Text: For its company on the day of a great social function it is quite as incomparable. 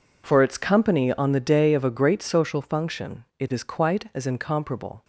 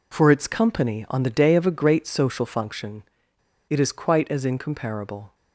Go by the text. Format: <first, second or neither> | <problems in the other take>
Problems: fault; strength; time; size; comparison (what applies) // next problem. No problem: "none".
first | pauses between "function" and "it"; noticeable; at 3.0 s; 0.66 s long